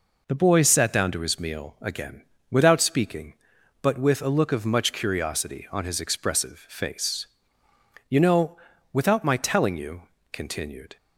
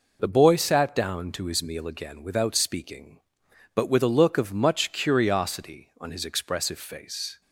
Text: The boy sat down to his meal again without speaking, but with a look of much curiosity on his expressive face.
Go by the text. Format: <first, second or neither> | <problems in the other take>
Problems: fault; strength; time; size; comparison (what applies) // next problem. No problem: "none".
second | pauses between "again" and "without"; slight; at 2.2 s; 0.28 s long // goes on to say "You know without my telling you continued"; strong; from 8.0 s on; 2.8 s long